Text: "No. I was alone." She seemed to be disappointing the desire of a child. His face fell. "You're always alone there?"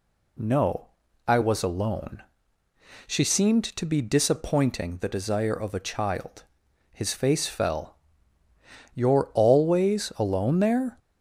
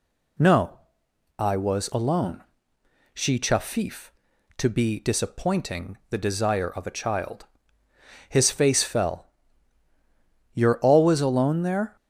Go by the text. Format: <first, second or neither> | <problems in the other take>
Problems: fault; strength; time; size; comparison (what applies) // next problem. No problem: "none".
first | says "chafif" for "seemed"; at 3.3 s